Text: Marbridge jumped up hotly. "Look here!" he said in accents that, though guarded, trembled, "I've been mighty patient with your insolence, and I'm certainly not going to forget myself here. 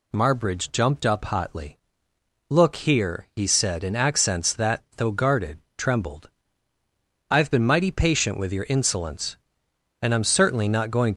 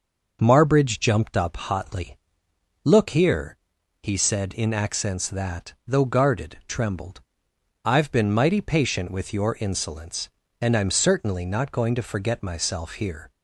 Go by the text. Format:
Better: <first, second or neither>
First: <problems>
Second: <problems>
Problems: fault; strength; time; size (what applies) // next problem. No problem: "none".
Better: second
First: stops before "to forget myself here"; at 11.1 s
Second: none